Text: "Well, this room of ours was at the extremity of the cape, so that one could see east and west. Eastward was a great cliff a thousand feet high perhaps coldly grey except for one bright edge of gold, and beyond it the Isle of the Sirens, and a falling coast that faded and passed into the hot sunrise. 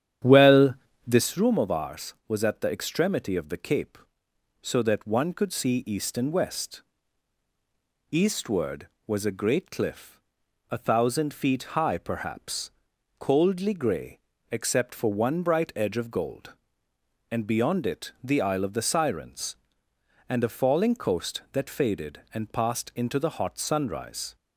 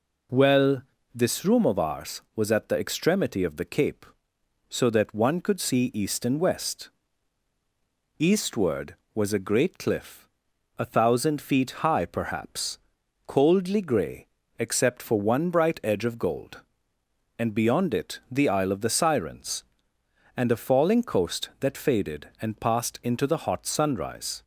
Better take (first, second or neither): second